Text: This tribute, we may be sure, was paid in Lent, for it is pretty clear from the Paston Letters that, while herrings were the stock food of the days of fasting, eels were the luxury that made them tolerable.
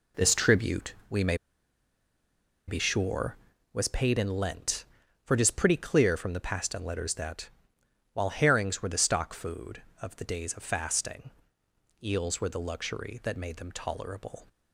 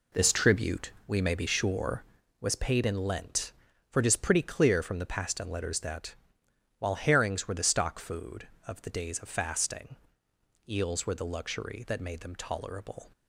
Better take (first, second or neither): second